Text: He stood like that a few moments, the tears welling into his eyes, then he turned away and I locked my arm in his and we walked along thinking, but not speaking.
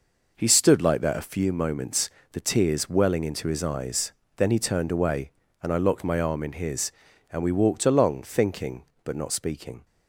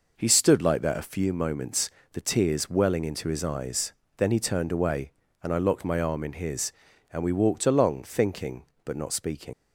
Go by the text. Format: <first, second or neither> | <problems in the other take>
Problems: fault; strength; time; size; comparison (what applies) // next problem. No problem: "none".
first | leaves "speaking" unfinished; at 9.5 s; 120 ms